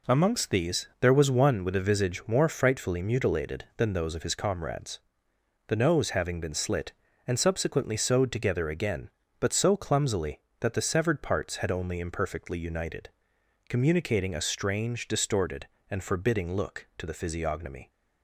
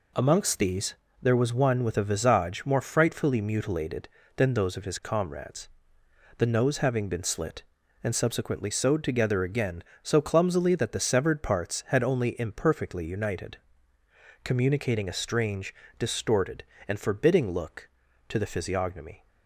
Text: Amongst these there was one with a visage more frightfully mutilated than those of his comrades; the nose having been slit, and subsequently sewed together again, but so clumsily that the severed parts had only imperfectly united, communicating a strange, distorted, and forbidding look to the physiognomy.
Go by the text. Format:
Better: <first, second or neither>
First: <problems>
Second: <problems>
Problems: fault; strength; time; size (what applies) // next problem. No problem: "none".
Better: first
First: none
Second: pauses between "these" and "there"; slight; at 0.9 s; 0.30 s long // skips "but"; at 9.9 s